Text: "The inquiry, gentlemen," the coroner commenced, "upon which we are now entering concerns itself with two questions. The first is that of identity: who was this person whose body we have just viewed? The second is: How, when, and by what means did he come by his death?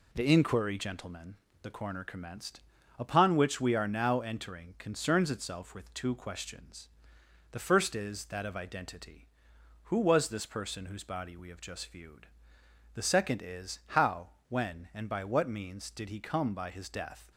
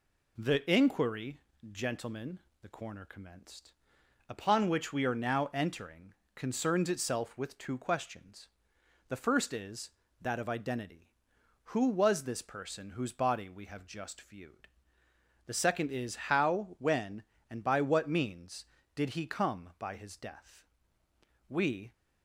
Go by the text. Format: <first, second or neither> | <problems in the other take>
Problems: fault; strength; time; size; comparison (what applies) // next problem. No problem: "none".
first | pauses between "entering" and "concerns"; slight; at 6.1 s; 0.22 s long // goes on to say "We"; slight; from 21.4 s on; 0.46 s long